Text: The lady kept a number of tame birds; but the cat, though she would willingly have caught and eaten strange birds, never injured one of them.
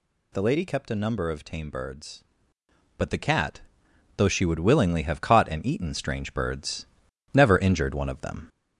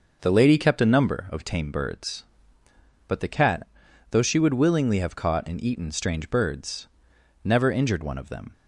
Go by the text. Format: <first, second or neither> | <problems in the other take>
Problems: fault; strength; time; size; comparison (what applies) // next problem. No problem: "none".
second | gets louder; slight; throughout; 2.5 dB